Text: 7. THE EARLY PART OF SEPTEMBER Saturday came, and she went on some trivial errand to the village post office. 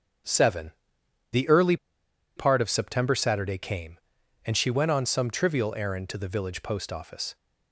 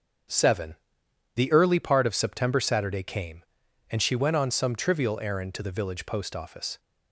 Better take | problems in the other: second | starts louder than the rest; strong; until 2.4 s; 7 dB; also in the second // pauses between "EARLY" and "PART"; noticeable; at 1.7 s; 0.60 s long

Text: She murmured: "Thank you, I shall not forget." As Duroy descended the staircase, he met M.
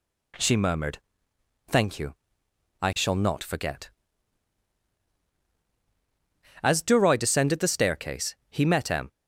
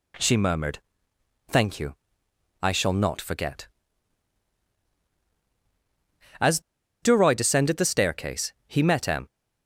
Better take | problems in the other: first | pauses between "As" and "Duroy"; at 6.5 s; 0.42 s long

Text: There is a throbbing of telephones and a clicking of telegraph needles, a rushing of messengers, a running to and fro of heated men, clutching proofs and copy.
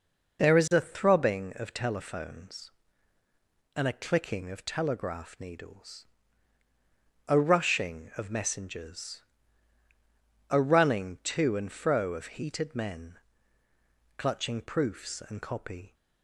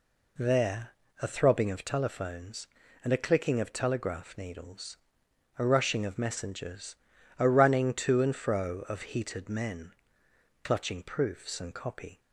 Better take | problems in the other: first | skips "is"; at 1.0 s

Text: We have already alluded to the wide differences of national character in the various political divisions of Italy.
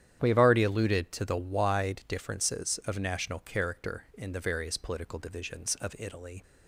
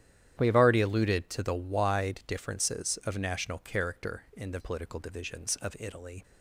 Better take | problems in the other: first | starts louder than the rest; strong; until 1.3 s; 11 dB; strong in the first // skips "various"; at 4.5 s

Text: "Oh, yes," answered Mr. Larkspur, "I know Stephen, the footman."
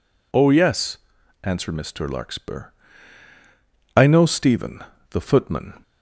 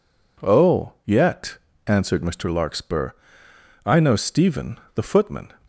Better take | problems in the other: first | says "yet" for "yes"; at 1.0 s

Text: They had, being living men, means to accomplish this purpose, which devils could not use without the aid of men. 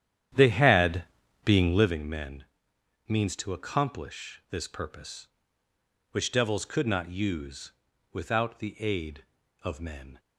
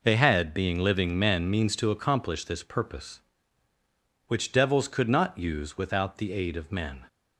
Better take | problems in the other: second | starts louder than the rest; strong; until 2.0 s; 10 dB // pauses between "use" and "without"; at 7.7 s; 0.42 s long

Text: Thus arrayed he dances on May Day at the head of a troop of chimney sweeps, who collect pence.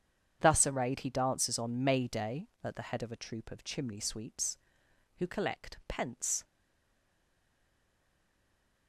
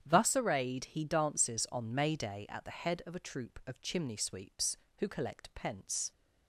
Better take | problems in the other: second | starts louder than the rest; strong; until 1.4 s; 8 dB; strong in the second // stays silent after the last word; from 6.4 s on; 2.4 s long

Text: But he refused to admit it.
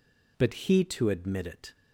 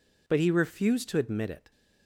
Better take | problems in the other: second | skips "refused"; at 0.8 s

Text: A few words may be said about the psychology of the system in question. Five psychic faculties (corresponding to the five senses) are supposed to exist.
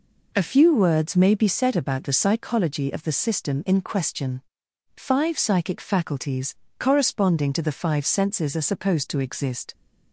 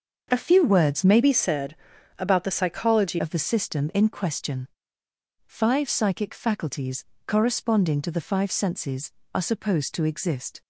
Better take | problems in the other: first | starts louder than the rest; until 1.3 s; 6.5 dB // changes voice from "be" to "psychology"; from 1.2 to 3.1 s; 1.9 s long // pauses between "said" and "about"; at 1.7 s; 0.42 s long

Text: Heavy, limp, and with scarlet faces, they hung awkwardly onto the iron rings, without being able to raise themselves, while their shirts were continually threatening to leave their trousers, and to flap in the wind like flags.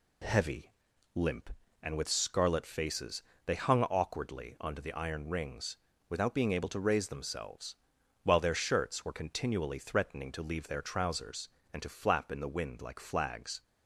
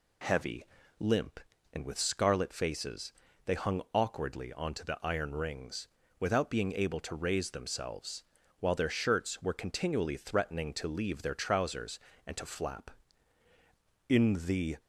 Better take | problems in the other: first | stops before "wind like flags"; at 14.7 s

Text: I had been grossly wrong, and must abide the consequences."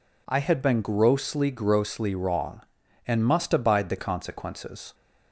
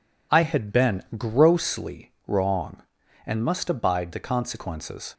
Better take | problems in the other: second | says "grossly" twice; at 1.5 s

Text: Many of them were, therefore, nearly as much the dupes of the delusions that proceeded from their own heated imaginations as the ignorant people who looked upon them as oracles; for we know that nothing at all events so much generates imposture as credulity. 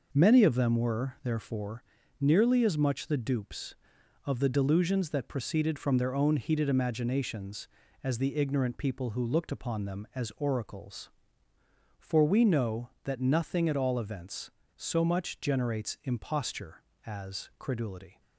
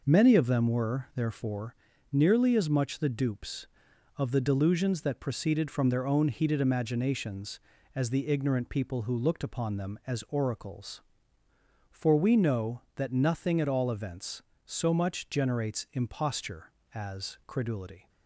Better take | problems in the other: neither | none

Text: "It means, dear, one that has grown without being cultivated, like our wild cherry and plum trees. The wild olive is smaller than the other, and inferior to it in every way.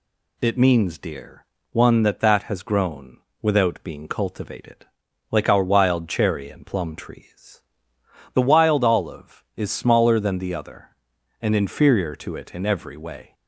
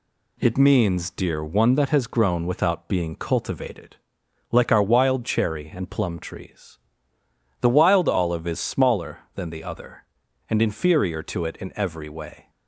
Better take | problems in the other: second | says "that" twice; at 2.1 s // pauses between "grown" and "without"; slight; at 3.1 s; 0.24 s long

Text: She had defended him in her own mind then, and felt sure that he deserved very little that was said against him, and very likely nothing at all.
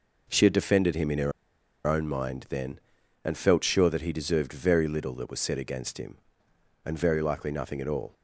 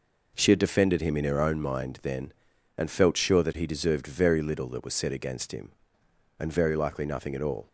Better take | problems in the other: second | pauses between "her" and "own"; noticeable; at 1.3 s; 0.55 s long

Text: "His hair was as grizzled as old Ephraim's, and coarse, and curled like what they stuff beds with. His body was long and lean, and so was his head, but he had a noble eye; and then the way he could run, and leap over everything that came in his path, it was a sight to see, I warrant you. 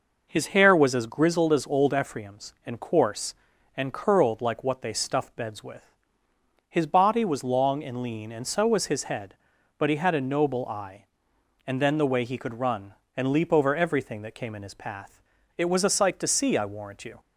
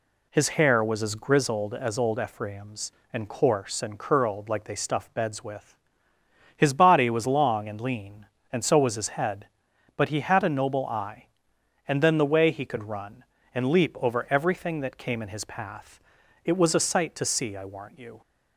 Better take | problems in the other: first | skips "what"; at 4.6 s

